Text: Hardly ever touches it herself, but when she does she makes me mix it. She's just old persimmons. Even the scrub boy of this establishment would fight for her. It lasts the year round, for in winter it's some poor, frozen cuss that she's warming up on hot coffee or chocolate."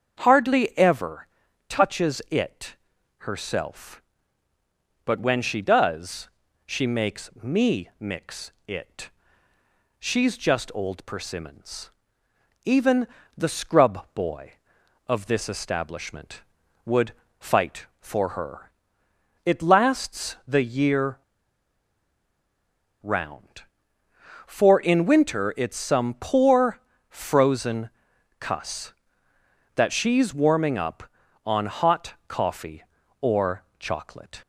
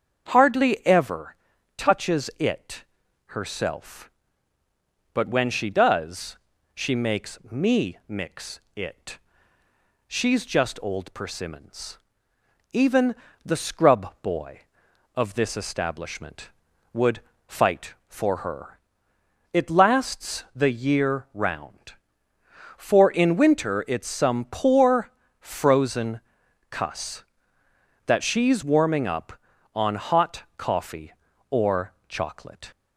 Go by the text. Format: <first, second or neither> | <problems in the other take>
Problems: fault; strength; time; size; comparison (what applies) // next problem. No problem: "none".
second | starts louder than the rest; strong; until 1.2 s; 7.5 dB; strong in the second // pauses between "ever" and "touches"; at 1.2 s; 0.40 s long; also in the second // pauses between "it" and "herself"; at 2.7 s; 0.44 s long; also in the second // pauses between "does" and "she"; at 6.2 s; 0.38 s long; also in the second // pauses between "mix" and "it"; slight; at 8.5 s; 0.16 s long; slight in the second // pauses between "Even" and "the"; slight; at 13.0 s; 0.30 s long; slight in the second // pauses between "would" and "fight"; slight; at 17.1 s; 0.26 s long; slight in the second // pauses between "year" and "round"; strong; at 21.1 s; 1.8 s long // pauses between "frozen" and "cuss"; noticeable; at 27.8 s; 0.50 s long; noticeable in the second // pauses between "or" and "chocolate"; slight; at 33.6 s; 0.16 s long; slight in the second